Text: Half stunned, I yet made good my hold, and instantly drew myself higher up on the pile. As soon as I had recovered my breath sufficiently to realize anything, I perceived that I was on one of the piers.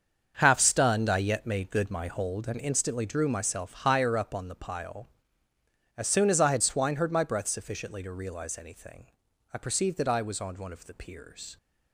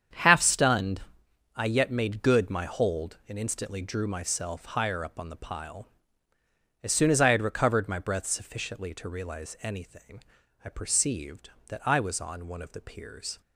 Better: second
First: starts louder than the rest; until 1.4 s; 7 dB // says "swineherd" for "recovered"; at 6.6 s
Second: starts louder than the rest; strong; until 1.7 s; 8 dB

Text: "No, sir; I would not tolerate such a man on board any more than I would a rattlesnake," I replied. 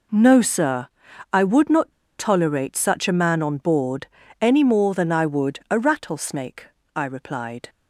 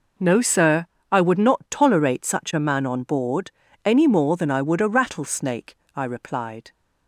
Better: second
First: pauses between "not" and "tolerate"; slight; at 1.9 s; 0.28 s long // pauses between "board" and "any"; slight; at 4.0 s; 0.34 s long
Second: pauses between "board" and "any"; slight; at 3.5 s; 0.34 s long

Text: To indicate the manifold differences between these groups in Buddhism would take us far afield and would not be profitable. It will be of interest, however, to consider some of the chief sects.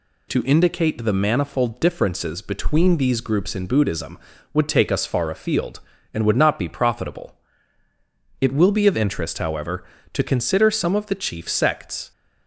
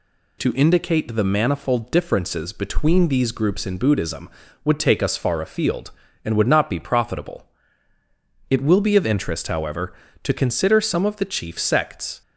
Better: neither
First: none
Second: none

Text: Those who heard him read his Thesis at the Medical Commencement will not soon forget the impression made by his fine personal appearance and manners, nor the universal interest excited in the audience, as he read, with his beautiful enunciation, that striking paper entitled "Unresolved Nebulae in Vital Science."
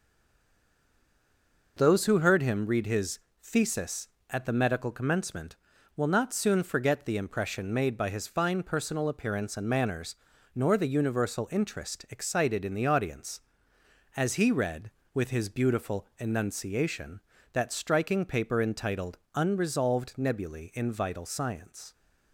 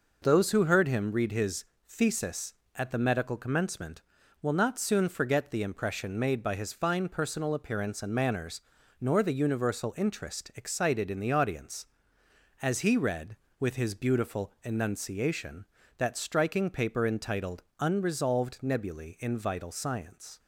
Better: second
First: stays silent before the first word; noticeable; until 1.7 s; 1.7 s long // pauses between "his" and "Thesis"; slight; at 3.1 s; 0.20 s long // pauses between "entitled" and "Unresolved"; slight; at 19.1 s; 0.16 s long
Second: pauses between "his" and "Thesis"; slight; at 1.6 s; 0.20 s long // pauses between "entitled" and "Unresolved"; slight; at 17.6 s; 0.16 s long

